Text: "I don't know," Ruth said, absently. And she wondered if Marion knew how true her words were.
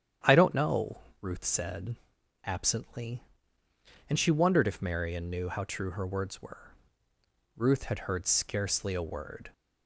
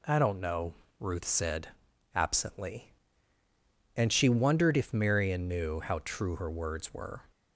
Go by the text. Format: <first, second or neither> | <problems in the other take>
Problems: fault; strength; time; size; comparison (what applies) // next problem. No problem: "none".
second | starts louder than the rest; strong; until 1.4 s; 9.5 dB // goes on to say "Ruth had heard scarcely a word"; strong; from 7.5 s on; 1.9 s long